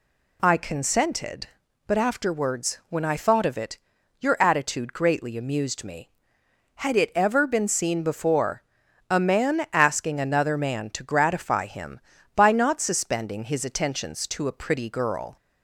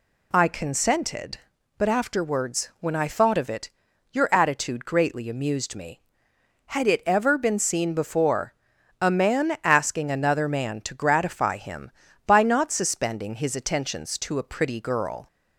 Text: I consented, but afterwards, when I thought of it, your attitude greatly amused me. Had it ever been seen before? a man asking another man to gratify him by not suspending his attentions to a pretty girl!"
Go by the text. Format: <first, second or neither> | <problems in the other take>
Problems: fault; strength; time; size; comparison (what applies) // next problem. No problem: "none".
neither | none